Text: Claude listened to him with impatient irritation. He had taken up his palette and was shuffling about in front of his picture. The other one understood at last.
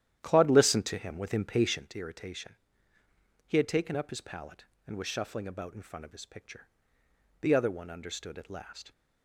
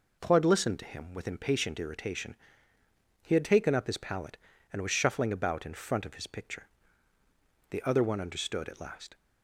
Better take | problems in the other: second | starts louder than the rest; strong; until 2.0 s; 11.5 dB

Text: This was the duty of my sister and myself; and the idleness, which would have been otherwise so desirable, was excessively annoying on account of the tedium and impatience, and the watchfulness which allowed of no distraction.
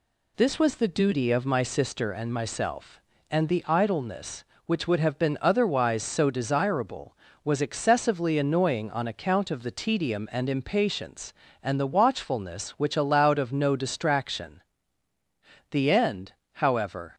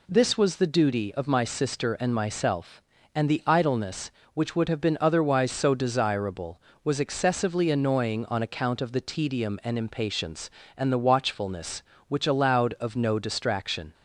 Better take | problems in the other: second | goes on to say "The end however"; from 15.7 s on; 1.4 s long

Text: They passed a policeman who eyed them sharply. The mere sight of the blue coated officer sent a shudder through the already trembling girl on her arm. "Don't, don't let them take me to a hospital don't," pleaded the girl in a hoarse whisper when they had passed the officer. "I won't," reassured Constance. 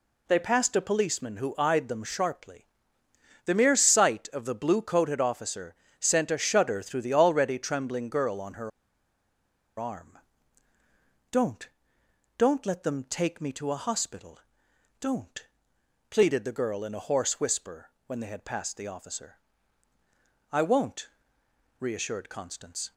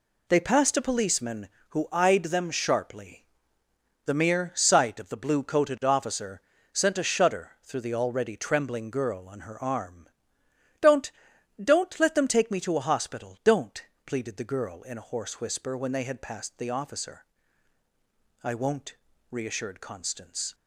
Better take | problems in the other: second | pauses between "officer" and "sent"; slight; at 5.7 s; 0.26 s long; slight in the second // pauses between "her" and "arm"; at 8.7 s; 1.0 s long // pauses between "hospital" and "don't"; noticeable; at 14.3 s; 0.62 s long // pauses between "whisper" and "when"; slight; at 17.8 s; 0.18 s long

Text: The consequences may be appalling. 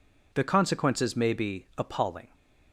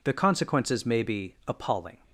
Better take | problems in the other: neither | none

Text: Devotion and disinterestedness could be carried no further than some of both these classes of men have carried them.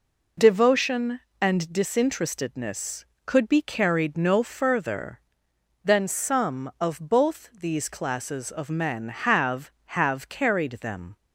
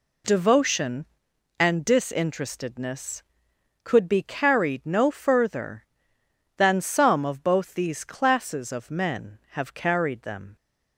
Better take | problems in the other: second | says "have" twice; at 9.8 s

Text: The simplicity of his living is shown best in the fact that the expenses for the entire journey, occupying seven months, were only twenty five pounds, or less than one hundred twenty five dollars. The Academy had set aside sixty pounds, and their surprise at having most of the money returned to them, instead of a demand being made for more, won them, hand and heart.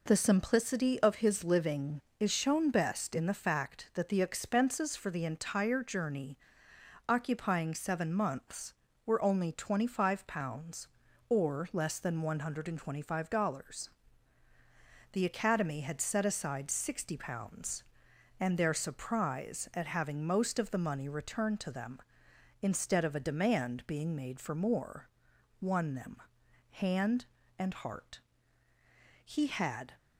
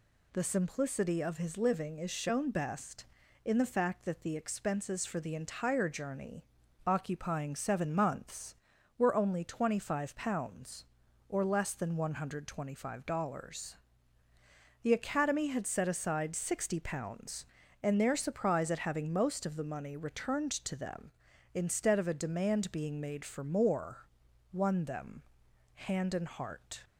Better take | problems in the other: second | goes on to say "He had"; noticeable; from 29.2 s on; 0.66 s long

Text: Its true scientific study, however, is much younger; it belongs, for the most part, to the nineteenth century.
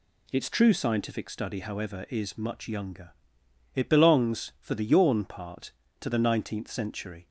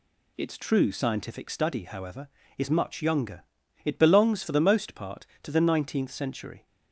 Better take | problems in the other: second | says "yawn" for "most"; at 4.8 s

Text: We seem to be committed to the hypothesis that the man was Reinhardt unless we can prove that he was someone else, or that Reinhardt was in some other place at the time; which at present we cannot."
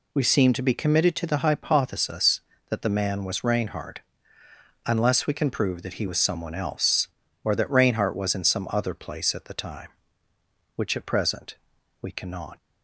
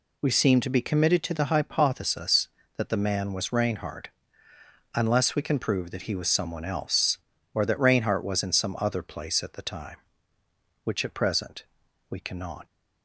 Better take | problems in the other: neither | pauses between "Reinhardt" and "unless"; noticeable; the same in both // pauses between "present" and "we"; the same in both

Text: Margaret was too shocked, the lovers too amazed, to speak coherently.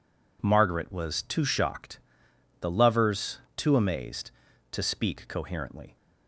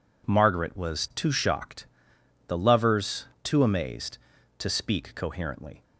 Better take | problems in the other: neither | pauses between "lovers" and "too"; slight; the same in both

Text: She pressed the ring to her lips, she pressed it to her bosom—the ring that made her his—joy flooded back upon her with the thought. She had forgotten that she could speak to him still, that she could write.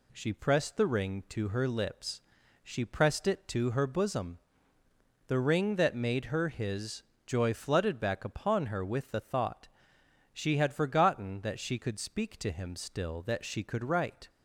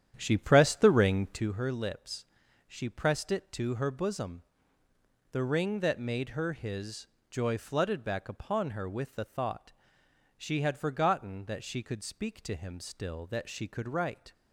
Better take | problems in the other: first | starts louder than the rest; strong; until 1.5 s; 10 dB

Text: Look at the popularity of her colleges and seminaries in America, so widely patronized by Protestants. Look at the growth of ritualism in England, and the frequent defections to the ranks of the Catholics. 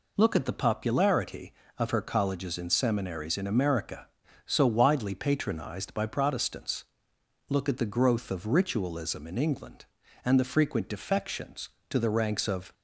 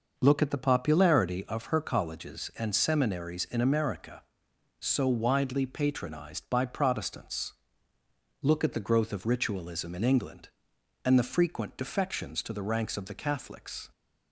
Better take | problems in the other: second | stops before "the Catholics"; at 12.7 s

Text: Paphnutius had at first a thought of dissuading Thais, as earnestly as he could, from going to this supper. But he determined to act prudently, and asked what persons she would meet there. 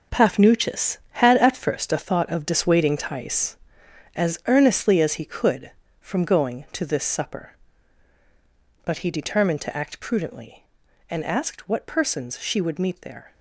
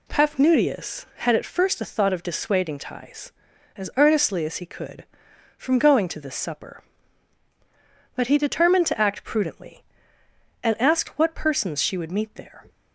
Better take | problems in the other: second | gets quieter; strong; throughout; 10 dB

